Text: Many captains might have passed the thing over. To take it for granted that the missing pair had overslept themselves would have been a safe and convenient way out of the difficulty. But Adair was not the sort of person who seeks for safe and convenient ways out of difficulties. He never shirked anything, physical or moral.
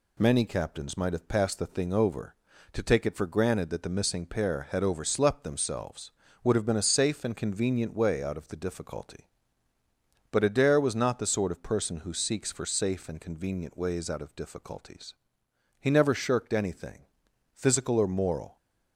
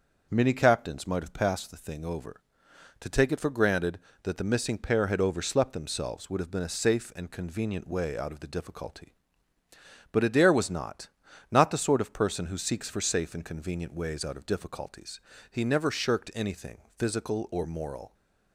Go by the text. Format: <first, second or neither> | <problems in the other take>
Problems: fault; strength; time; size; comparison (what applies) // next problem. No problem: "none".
first | starts louder than the rest; until 1.3 s; 6.5 dB // says "not" twice; at 11.5 s